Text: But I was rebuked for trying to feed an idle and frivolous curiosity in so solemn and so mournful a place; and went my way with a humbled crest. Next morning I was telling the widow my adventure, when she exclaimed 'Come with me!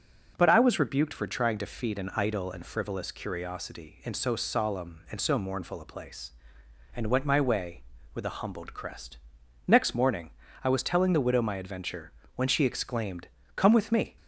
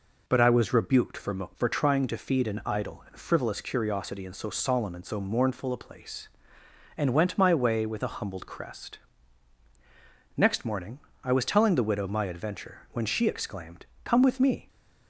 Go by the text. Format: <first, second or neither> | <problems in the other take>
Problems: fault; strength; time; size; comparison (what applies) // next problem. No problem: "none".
first | says "for" twice; at 1.5 s // pauses between "morning" and "I"; slight; at 10.9 s; 0.24 s long; slight in the first // pauses between "exclaimed" and "Come"; slight; at 13.8 s; 0.18 s long; slight in the first